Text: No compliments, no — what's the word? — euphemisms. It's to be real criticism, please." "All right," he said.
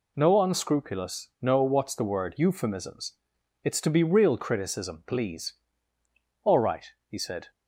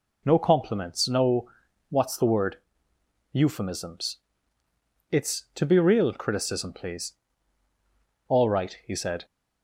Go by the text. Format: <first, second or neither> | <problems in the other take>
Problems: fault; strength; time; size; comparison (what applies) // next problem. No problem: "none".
second | says "unscrupulous" for "compliments"; at 0.4 s